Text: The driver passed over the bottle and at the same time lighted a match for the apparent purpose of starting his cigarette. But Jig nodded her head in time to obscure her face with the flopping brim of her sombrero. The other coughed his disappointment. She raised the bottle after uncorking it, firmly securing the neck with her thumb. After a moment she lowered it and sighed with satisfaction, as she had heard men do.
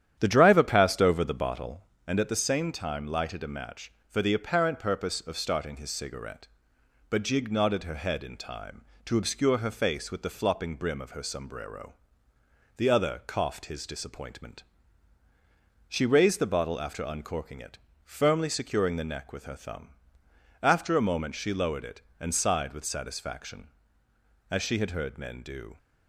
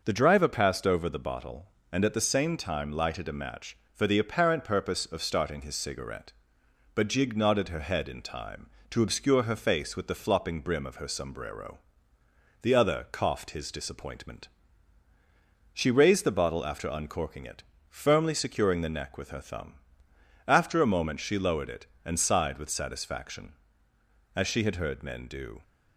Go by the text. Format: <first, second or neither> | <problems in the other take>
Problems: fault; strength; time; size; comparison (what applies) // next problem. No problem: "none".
second | starts louder than the rest; strong; until 1.9 s; 10 dB